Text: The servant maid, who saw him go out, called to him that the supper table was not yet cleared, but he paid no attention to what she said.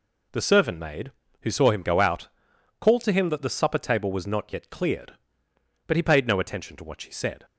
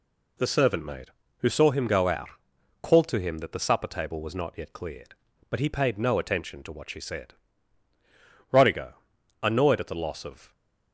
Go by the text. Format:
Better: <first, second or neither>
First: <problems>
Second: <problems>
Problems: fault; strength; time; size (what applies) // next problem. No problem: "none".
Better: first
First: none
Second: goes on to say "Rodigo annoyed at the loss of"; strong; from 8.5 s on; 2.0 s long